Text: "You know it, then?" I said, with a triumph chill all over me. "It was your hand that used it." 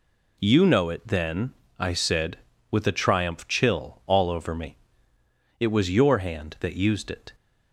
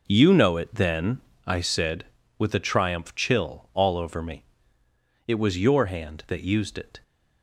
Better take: first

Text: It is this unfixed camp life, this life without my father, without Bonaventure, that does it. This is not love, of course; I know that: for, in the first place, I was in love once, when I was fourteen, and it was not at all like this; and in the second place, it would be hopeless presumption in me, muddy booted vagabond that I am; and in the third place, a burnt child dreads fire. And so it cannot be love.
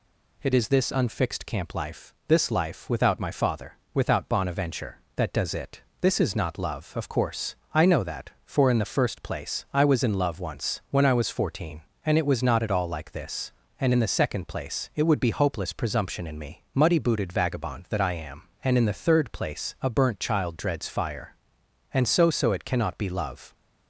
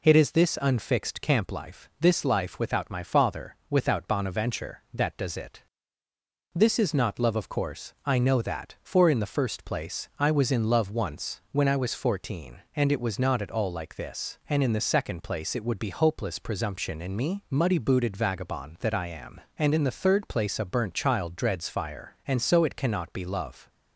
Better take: second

